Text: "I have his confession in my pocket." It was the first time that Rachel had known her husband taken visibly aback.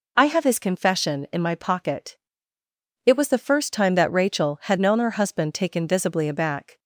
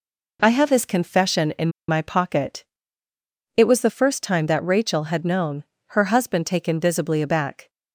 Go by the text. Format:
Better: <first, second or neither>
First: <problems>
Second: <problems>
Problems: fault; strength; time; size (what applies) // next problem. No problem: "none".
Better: first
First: none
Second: pauses between "in" and "my"; slight; at 1.6 s; 0.19 s long // pauses between "known" and "her"; slight; at 5.6 s; 0.30 s long